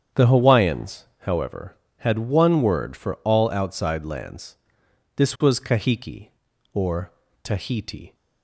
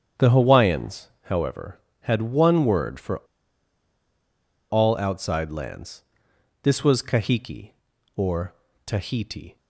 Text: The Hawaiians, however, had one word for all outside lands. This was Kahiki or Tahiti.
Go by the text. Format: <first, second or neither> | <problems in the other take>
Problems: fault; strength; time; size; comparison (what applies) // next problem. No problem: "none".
first | starts louder than the rest; strong; until 1.3 s; 8.5 dB; strong in the first // pauses between "for" and "all"; strong; at 3.1 s; 1.5 s long // pauses between "or" and "Tahiti"; slight; at 8.5 s; 0.32 s long; slight in the first